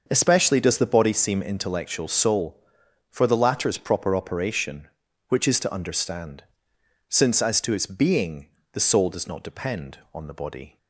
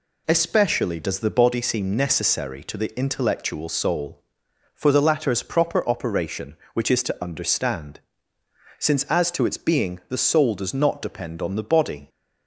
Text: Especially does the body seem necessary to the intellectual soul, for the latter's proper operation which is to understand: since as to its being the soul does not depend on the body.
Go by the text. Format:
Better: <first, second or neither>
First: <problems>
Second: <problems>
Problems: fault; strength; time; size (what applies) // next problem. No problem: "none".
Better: second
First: starts louder than the rest; until 1.0 s; 6 dB // skips "necessary to the"; at 1.4 s // pauses between "being" and "the"; slight; at 8.4 s; 0.24 s long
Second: none